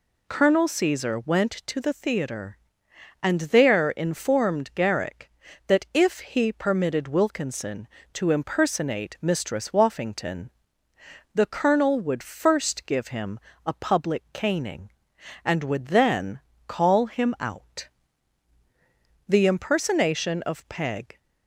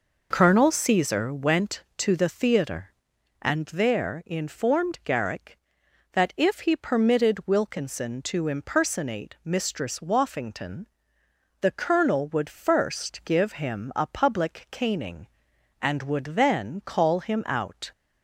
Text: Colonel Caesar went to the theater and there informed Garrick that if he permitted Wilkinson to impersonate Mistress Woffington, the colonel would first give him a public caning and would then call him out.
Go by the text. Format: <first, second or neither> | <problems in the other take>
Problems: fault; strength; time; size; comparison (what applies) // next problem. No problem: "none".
second | pauses between "him" and "a"; slight; at 13.3 s; 0.28 s long // pauses between "then" and "call"; slight; at 16.3 s; 0.26 s long // goes on to say "The impersonation of Peg"; strong; from 19.2 s on; 1.9 s long